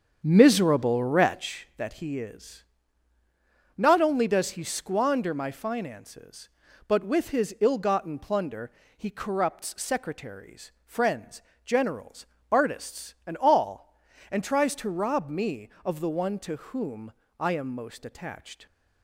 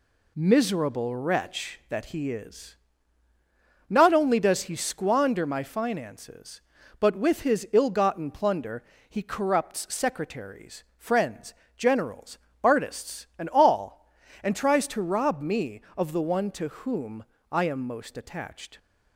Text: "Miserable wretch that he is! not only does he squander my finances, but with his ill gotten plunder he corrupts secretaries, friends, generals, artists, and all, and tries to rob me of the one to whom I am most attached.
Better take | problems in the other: second | starts louder than the rest; strong; until 1.5 s; 7.5 dB // pauses between "plunder" and "he"; slight; at 8.6 s; 0.28 s long; slight in the second // pauses between "whom" and "I"; slight; at 17.1 s; 0.24 s long; slight in the second

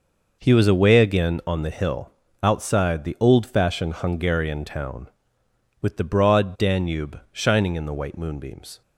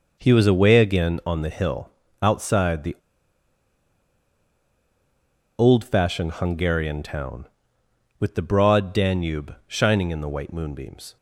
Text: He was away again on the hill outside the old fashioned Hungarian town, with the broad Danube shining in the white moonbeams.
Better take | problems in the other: first | pauses between "hill" and "outside"; slight; at 1.8 s; 0.34 s long; slight in the first // pauses between "the" and "old"; strong; at 2.9 s; 2.6 s long

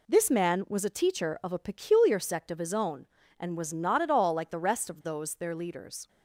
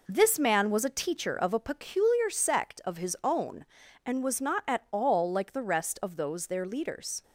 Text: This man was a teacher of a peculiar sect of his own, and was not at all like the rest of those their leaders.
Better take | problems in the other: neither | none

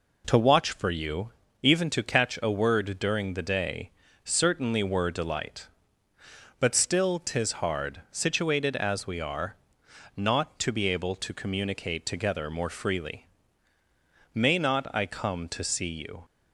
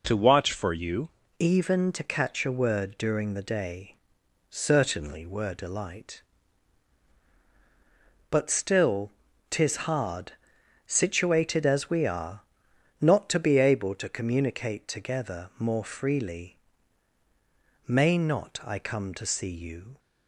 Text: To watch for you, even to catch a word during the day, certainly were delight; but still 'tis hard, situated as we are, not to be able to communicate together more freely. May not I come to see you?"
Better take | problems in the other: first | changes voice at "even"; from 1.3 s on; 18.6 s long // pauses between "still" and "tis"; slight; at 9.1 s; 0.36 s long

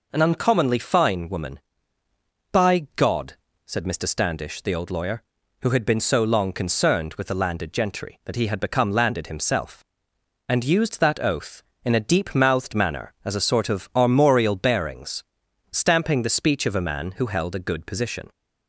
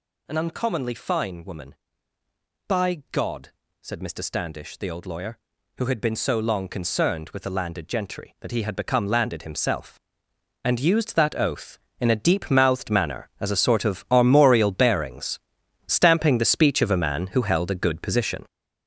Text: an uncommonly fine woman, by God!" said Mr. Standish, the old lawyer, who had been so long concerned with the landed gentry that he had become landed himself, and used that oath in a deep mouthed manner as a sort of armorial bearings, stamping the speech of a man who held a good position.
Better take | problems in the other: first | gets louder; strong; throughout; 8 dB

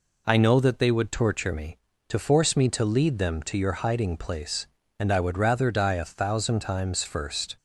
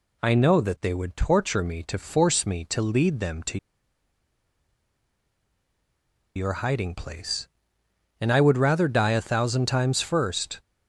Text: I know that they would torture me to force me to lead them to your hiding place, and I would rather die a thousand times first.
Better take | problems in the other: first | pauses between "to" and "your"; strong; at 3.5 s; 2.7 s long

